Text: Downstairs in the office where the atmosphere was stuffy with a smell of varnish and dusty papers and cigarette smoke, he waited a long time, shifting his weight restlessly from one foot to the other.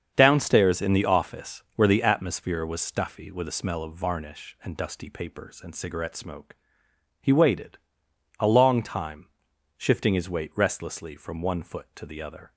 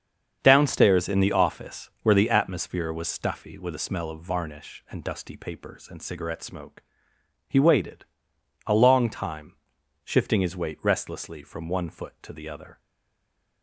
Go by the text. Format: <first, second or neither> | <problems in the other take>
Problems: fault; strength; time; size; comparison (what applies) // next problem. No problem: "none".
first | starts louder than the rest; strong; until 1.4 s; 7 dB; strong in the first // pauses between "waited" and "a"; noticeable; at 8.0 s; 0.60 s long; noticeable in the first // stays silent after the last word; slight; from 12.7 s on; 0.9 s long